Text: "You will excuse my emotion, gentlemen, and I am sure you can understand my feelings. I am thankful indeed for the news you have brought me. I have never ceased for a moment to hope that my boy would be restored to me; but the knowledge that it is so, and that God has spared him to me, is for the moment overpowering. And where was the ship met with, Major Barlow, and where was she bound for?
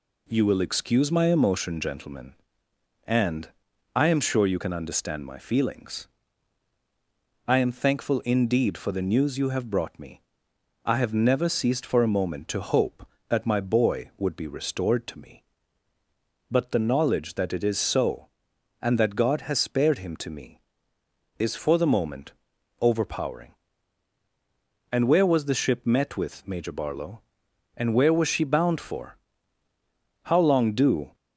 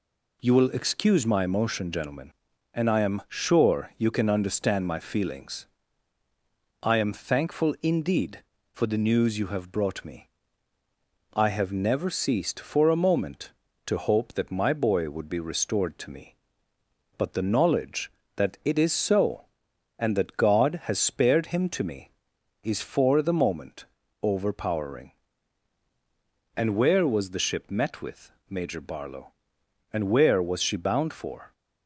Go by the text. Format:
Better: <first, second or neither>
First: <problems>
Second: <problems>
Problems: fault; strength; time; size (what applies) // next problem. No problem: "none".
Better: second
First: pauses between "and" and "I"; noticeable; at 3.4 s; 0.46 s long // pauses between "moment" and "overpowering"; noticeable; at 22.3 s; 0.48 s long // goes on to say "How long do"; noticeable; from 30.2 s on; 0.92 s long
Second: pauses between "moment" and "overpowering"; slight; at 23.8 s; 0.36 s long